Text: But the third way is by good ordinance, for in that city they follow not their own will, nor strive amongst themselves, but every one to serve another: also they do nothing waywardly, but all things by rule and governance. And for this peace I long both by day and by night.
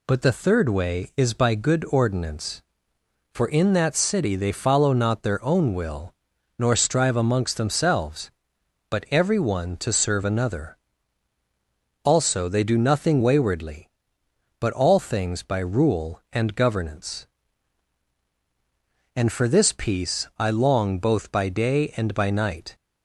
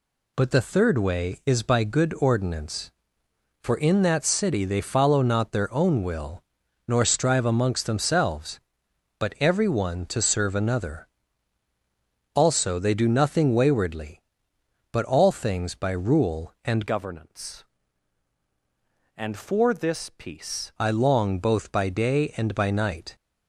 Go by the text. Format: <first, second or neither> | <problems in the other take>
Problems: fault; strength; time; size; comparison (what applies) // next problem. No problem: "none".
first | changes voice from "governance" to "peace"; from 16.8 to 20.7 s; 3.9 s long